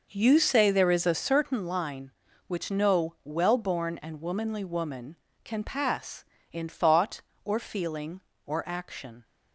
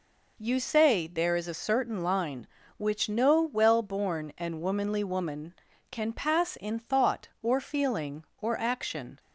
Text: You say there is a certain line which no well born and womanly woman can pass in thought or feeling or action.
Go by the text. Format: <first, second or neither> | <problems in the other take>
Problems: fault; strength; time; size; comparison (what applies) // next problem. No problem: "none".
second | starts louder than the rest; noticeable; until 1.6 s; 5.5 dB